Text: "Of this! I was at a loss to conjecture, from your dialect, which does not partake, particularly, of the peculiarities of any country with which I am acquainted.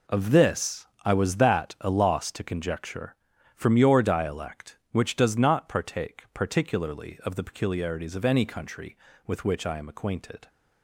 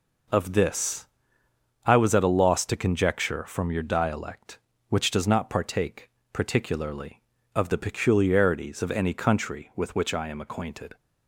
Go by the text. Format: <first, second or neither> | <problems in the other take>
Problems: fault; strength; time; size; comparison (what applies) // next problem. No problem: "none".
second | says "that" for "at"; at 1.3 s